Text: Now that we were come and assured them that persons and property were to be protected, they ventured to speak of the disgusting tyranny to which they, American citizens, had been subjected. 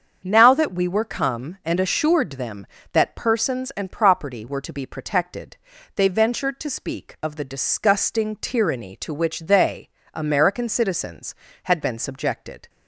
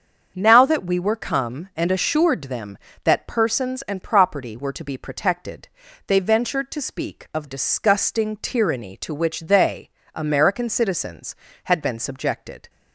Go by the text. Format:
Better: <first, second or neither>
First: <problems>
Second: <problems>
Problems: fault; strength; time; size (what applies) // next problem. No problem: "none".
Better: first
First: starts louder than the rest; until 1.2 s; 7 dB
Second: starts louder than the rest; until 1.3 s; 7 dB // skips "the"; at 7.4 s